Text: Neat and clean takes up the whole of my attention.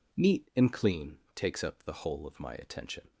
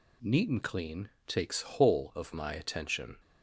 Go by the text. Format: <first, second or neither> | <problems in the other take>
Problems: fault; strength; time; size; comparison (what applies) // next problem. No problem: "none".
first | pauses between "clean" and "takes"; slight; at 1.0 s; 0.20 s long; slight in the first // skips "up the"; at 1.6 s